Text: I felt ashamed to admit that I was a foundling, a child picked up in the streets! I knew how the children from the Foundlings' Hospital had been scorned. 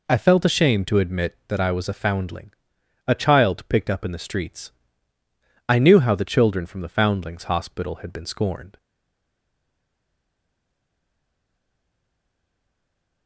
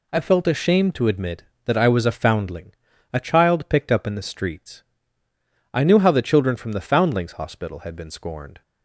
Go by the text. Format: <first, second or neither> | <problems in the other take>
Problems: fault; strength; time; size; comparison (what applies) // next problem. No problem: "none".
second | stays silent after the last word; strong; from 8.7 s on; 4.5 s long